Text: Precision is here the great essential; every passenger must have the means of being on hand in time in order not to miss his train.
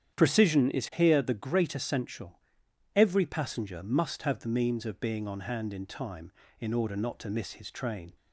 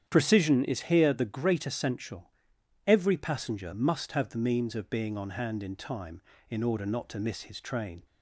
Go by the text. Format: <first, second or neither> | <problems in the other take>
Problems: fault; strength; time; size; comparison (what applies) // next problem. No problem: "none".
neither | starts louder than the rest; strong; the same in both